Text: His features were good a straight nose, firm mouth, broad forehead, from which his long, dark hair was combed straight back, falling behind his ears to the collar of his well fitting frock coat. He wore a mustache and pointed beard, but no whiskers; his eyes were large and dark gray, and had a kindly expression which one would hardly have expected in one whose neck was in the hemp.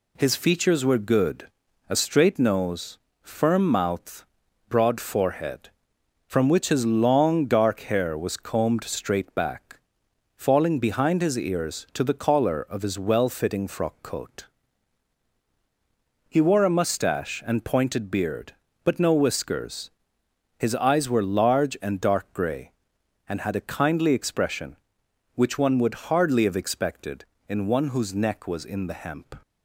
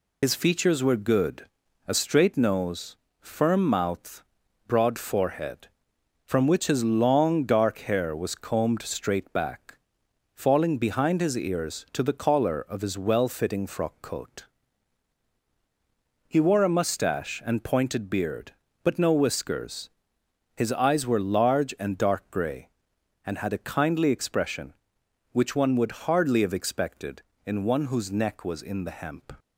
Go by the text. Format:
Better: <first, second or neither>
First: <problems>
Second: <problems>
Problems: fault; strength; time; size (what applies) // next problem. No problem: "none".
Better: first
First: pauses between "good" and "a"; at 1.4 s; 0.42 s long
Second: loses the start of "His"; at 0.2 s; 85 ms // pauses between "good" and "a"; at 1.4 s; 0.42 s long